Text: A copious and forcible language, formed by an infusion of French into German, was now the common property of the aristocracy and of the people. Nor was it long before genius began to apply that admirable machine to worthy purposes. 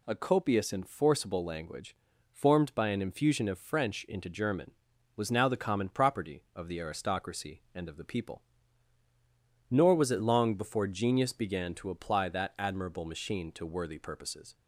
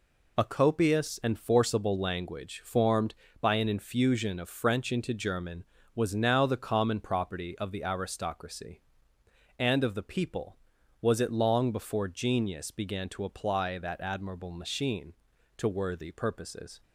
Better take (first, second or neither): first